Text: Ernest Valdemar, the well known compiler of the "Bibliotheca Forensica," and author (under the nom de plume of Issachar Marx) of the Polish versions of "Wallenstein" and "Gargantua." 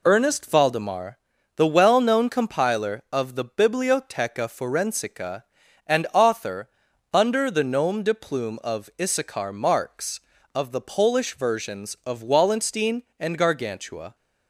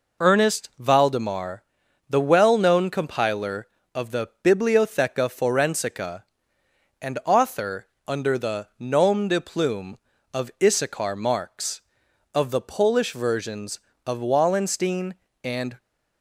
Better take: first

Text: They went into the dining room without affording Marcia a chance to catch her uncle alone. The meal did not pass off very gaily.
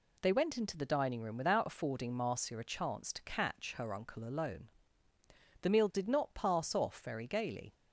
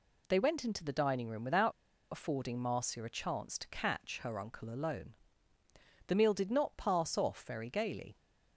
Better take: first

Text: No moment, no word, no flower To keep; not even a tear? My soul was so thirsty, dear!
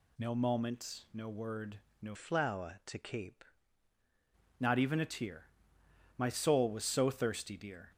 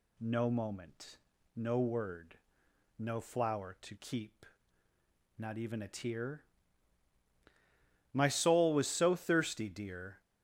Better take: second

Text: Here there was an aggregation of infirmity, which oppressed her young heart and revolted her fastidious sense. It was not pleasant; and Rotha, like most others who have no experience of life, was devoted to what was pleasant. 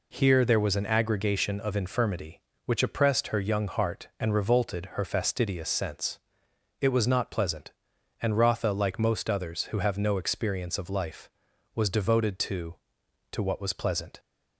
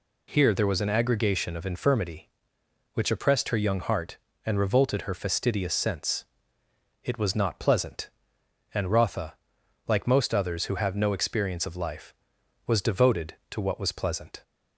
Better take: second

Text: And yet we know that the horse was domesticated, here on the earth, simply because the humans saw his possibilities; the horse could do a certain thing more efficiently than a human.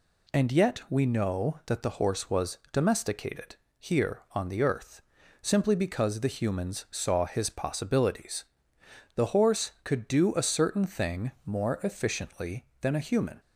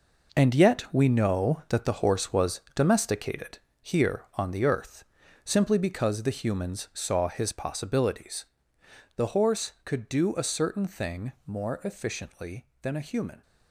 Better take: first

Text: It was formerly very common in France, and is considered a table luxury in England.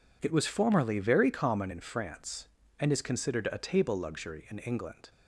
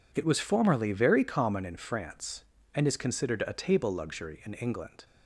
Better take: neither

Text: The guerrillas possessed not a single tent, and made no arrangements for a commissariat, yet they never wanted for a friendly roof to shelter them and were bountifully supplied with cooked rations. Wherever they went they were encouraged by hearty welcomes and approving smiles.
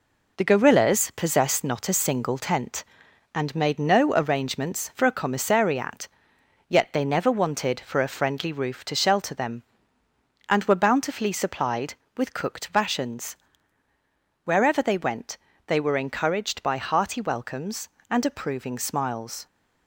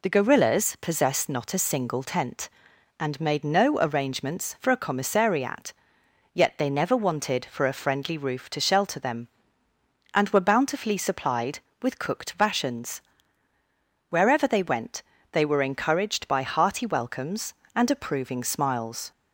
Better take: second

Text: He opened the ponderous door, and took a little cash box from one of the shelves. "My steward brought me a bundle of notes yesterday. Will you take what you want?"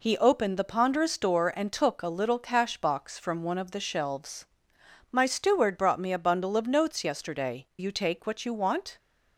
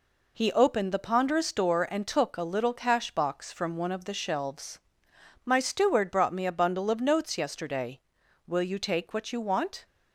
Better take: second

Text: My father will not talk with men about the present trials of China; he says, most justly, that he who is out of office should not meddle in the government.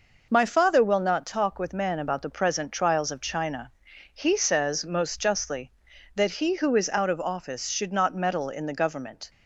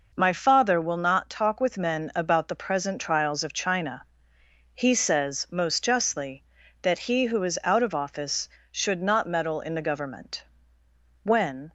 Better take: first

